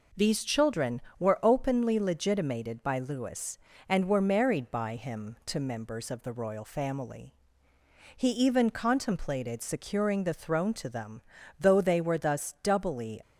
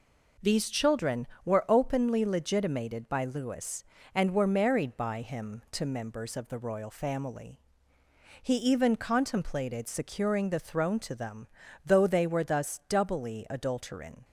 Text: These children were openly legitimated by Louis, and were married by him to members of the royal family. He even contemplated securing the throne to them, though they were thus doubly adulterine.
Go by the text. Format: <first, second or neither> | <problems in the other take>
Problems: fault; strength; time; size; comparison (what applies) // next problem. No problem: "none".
second | stops before "adulterine"; at 13.2 s